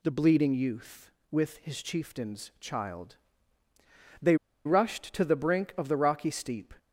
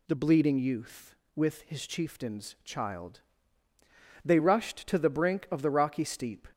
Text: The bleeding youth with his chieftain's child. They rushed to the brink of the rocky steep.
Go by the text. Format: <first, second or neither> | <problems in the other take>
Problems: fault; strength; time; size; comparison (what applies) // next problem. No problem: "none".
second | pauses between "They" and "rushed"; slight; at 4.3 s; 0.30 s long